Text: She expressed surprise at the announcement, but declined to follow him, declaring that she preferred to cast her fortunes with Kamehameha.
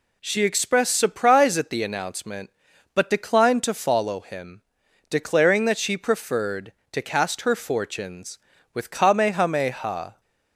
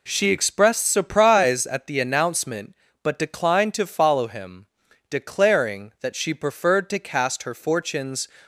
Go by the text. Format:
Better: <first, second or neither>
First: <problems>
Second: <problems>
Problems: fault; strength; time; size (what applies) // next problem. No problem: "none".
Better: first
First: none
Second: stops before "with Kamehameha"; at 8.4 s